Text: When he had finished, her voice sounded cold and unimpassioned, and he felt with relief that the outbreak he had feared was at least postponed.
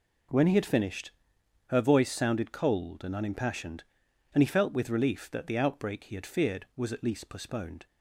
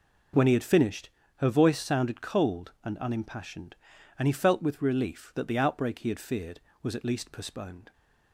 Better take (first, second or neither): neither